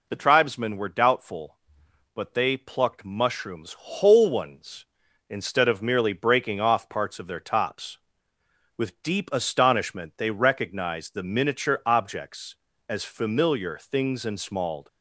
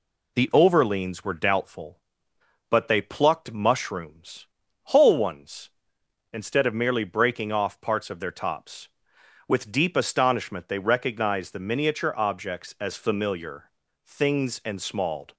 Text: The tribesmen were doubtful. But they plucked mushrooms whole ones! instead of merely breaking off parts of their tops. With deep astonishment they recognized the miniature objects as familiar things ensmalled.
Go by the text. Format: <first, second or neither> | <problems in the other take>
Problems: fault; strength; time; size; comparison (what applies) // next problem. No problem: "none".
first | says "overleans" for "tribesmen"; at 0.5 s // pauses between "mushrooms" and "whole"; at 4.4 s; 0.42 s long // pauses between "familiar" and "things"; slight; at 13.6 s; 0.34 s long